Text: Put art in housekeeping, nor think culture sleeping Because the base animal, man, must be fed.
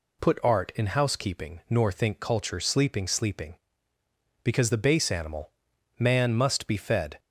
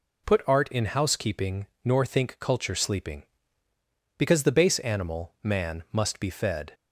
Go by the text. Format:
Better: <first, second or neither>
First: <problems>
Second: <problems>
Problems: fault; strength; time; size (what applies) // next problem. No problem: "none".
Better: second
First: says "sleeping" twice; at 3.0 s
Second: none